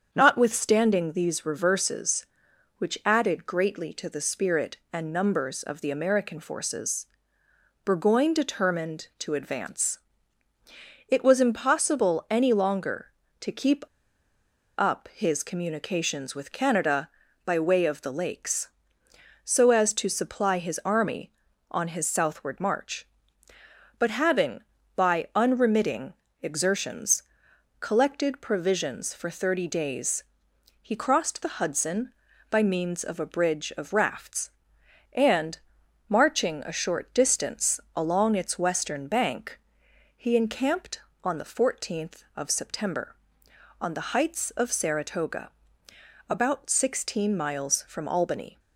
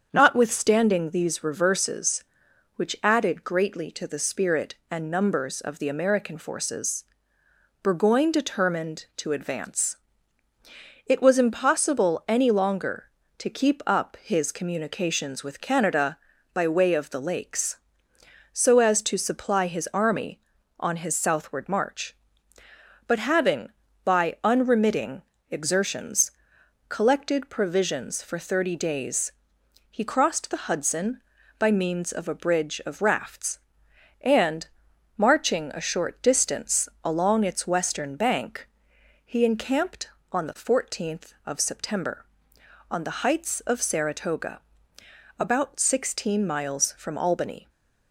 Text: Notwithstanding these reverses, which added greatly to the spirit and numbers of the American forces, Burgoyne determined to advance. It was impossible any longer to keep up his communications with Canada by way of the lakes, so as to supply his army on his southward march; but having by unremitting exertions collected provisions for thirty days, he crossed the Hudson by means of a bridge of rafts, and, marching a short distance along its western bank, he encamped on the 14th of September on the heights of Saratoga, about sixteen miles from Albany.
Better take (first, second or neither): second